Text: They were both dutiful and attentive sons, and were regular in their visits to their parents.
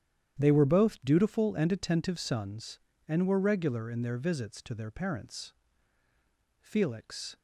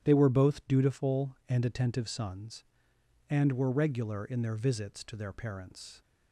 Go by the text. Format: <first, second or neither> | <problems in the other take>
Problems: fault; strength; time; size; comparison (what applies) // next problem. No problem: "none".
second | starts louder than the rest; strong; until 1.4 s; 10 dB; strong in the second // goes on to say "Felix"; noticeable; from 6.6 s on; 0.76 s long